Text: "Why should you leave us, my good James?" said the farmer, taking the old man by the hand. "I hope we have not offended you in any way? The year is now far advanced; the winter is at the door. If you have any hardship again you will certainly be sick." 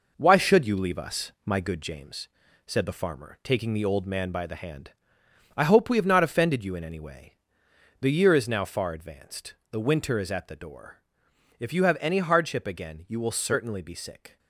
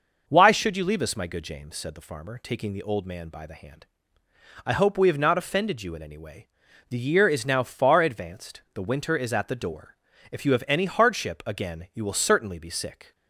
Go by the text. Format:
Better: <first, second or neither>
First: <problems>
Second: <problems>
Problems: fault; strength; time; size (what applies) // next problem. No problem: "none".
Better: second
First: gets quieter; noticeable; throughout; 5.5 dB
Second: none